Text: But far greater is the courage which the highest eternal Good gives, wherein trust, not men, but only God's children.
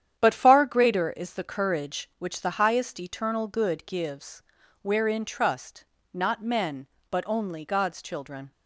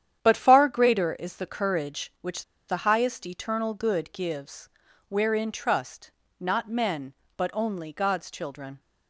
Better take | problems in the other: first | starts louder than the rest; strong; until 1.2 s; 9.5 dB; strong in the first // pauses between "which" and "the"; slight; at 2.4 s; 0.24 s long

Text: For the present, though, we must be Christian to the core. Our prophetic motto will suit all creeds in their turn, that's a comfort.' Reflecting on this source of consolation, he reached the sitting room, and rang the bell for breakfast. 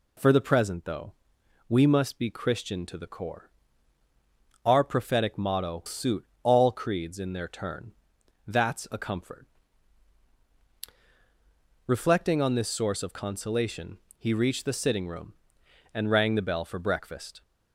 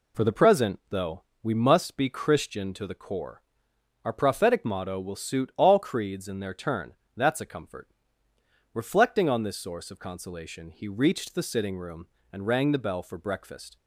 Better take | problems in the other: second | skips "will"; at 5.8 s // pauses between "suit" and "all"; slight; at 6.2 s; 0.16 s long

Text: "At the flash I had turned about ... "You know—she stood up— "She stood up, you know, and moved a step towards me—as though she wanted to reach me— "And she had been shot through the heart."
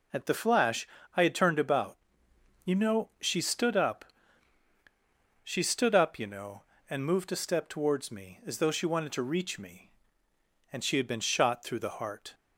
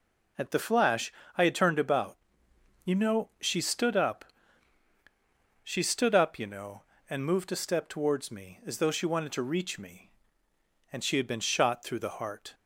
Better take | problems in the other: neither | pauses between "flash" and "I"; slight; the same in both

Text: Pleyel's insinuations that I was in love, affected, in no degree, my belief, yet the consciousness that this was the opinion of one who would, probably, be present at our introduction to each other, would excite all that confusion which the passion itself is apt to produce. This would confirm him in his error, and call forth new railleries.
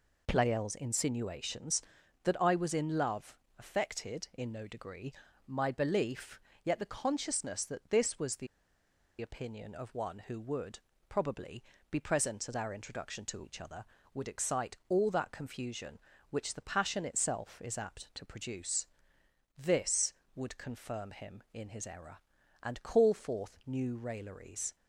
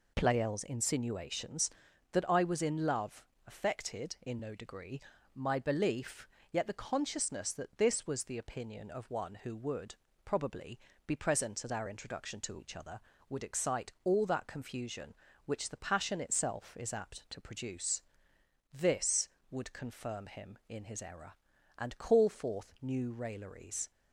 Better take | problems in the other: second | pauses between "the" and "opinion"; noticeable; at 8.4 s; 0.74 s long

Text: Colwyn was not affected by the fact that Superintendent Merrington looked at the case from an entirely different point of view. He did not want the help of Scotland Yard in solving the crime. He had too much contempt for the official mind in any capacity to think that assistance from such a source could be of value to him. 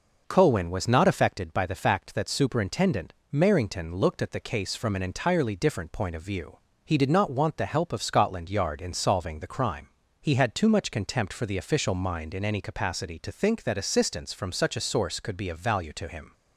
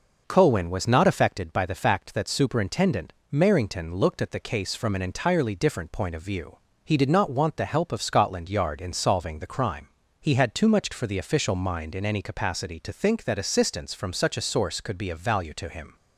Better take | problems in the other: first | pauses between "Superintendent" and "Merrington"; slight; at 3.1 s; 0.20 s long; slight in the first // skips "contempt"; at 10.9 s

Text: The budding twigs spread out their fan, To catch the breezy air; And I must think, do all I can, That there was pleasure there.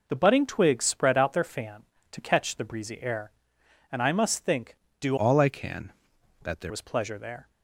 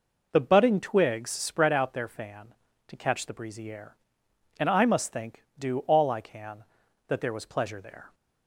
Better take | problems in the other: second | changes voice from "all" to "there"; from 5.1 to 6.7 s; 1.6 s long

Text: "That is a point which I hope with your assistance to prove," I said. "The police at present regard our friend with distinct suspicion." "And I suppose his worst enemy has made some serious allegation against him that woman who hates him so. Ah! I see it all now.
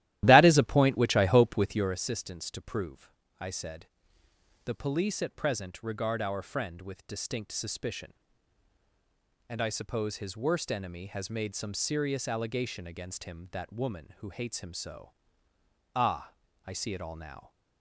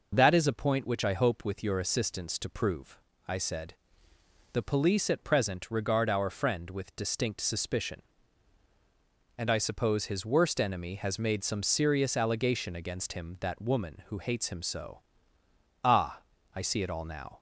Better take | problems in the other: second | starts louder than the rest; strong; until 2.0 s; 14 dB

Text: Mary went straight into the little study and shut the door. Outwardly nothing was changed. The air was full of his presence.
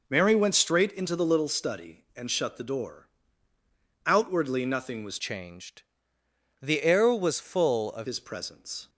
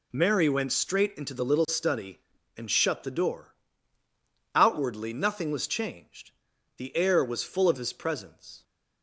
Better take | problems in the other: second | changes voice from "changed" to "of"; from 5.1 to 8.0 s; 2.9 s long

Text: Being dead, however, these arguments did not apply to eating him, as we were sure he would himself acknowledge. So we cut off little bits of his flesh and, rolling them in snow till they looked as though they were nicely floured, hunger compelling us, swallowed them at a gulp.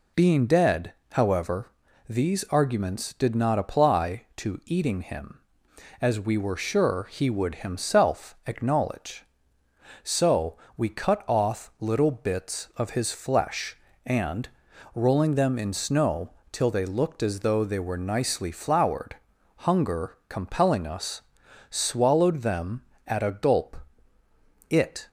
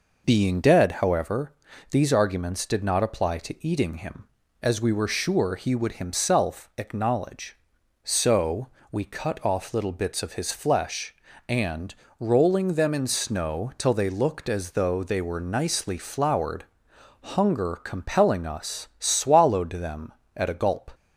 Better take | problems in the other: second | pauses between "So" and "we"; slight; at 10.5 s; 0.20 s long; slight in the second // pauses between "snow" and "till"; slight; at 16.2 s; 0.22 s long // goes on to say "It"; slight; from 24.6 s on; 0.38 s long

